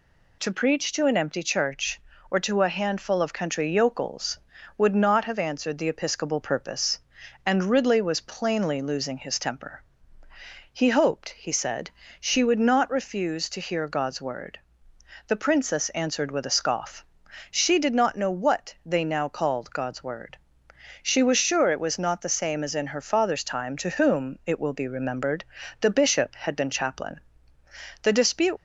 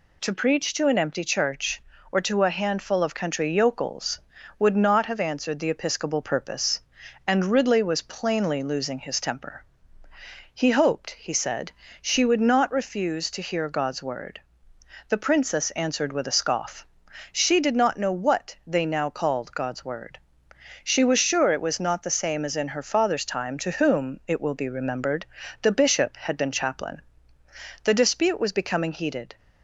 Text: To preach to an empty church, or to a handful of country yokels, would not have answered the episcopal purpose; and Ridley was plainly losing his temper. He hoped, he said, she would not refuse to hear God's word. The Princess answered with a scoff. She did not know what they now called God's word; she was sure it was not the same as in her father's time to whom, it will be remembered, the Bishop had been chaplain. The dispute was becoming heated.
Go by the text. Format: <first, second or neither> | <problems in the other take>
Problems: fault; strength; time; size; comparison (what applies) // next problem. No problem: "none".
second | stops before "was becoming heated"; at 28.5 s